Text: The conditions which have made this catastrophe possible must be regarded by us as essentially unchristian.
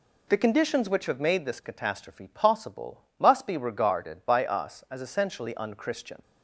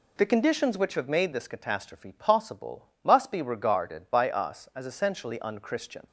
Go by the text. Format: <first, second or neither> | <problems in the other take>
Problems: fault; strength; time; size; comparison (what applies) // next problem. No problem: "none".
neither | pauses between "possible" and "must"; slight; the same in both